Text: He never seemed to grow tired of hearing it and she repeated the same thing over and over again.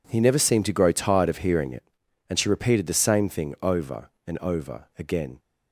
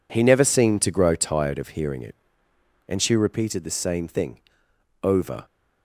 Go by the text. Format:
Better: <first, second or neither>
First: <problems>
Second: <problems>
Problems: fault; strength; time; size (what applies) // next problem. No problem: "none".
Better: first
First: none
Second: pauses between "thing" and "over"; noticeable; at 4.4 s; 0.64 s long // stops before "and over again"; at 5.4 s